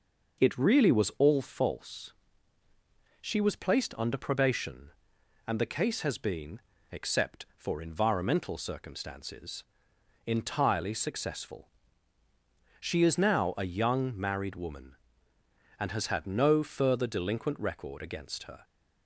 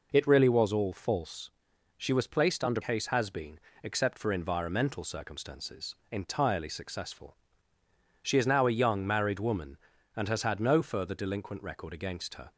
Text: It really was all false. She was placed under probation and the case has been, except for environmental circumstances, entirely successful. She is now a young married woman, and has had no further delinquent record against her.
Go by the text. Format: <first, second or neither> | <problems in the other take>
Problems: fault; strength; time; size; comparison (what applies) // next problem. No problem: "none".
first | skips "probation and the"; at 2.8 s